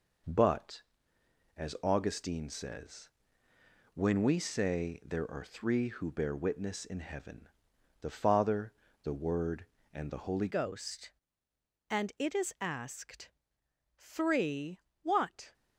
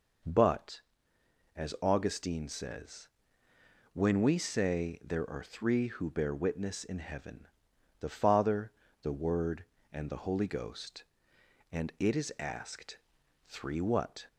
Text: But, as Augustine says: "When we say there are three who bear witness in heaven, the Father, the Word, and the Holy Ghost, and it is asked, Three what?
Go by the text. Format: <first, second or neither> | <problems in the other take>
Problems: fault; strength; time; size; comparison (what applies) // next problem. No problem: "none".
second | changes voice at "Ghost"; from 10.4 s on; 5.1 s long // pauses between "Three" and "what"; slight; at 14.7 s; 0.24 s long